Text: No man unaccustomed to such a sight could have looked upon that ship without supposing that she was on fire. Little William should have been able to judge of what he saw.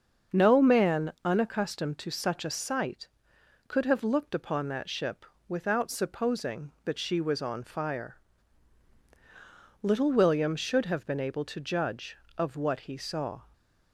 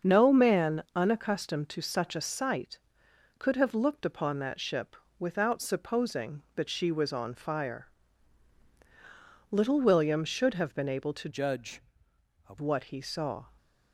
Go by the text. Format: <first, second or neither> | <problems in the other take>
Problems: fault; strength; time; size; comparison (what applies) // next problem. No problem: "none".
first | starts louder than the rest; until 1.1 s; 6.5 dB; also in the first // pauses between "ship" and "without"; slight; at 4.9 s; 0.22 s long; slight in the first // changes voice from "judge" to "of"; from 11.2 to 12.5 s; 1.3 s long